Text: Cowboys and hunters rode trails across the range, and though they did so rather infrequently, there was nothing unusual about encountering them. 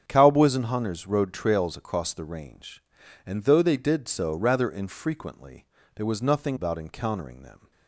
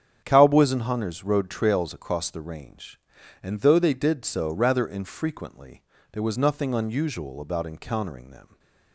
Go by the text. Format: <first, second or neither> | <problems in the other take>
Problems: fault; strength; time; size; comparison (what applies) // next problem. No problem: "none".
second | starts louder than the rest; strong; until 1.0 s; 7.5 dB; strong in the second // skips "unusual"; at 6.5 s